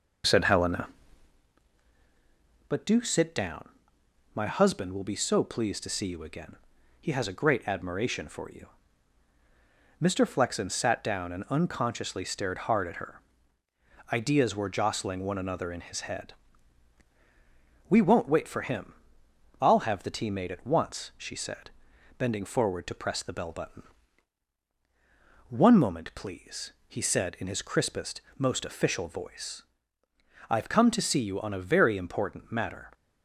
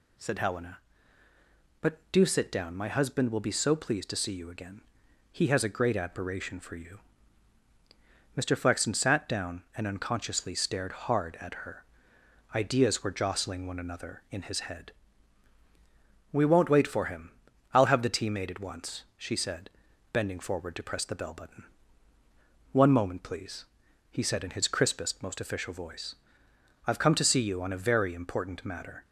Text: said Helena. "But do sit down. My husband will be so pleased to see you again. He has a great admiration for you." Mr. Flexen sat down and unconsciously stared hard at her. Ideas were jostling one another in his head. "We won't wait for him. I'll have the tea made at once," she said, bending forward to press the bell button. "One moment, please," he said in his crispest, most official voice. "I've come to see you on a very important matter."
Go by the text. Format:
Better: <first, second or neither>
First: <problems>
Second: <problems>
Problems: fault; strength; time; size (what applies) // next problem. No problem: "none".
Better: second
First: starts louder than the rest; noticeable; until 1.5 s; 5 dB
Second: none